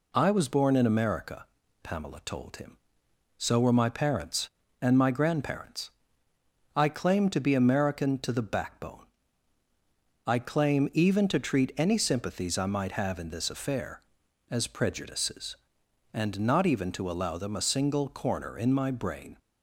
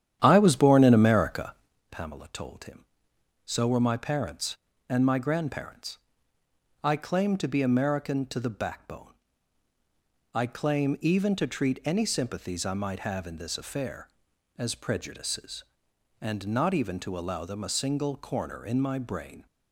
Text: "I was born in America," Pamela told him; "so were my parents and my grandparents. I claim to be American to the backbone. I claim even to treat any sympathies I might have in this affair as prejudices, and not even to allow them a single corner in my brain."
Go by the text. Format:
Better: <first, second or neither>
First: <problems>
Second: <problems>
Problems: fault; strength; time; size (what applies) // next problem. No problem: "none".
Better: first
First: none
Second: starts louder than the rest; strong; until 1.8 s; 10.5 dB